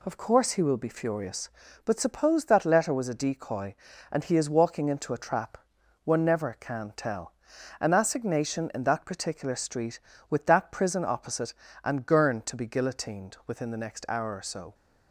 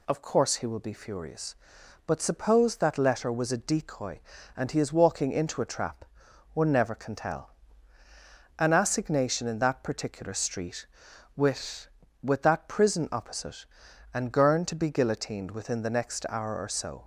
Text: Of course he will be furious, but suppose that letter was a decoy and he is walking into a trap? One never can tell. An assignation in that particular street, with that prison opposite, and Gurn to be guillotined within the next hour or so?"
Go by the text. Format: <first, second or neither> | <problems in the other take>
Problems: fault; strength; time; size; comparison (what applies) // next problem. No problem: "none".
first | says "with" twice; at 12.2 s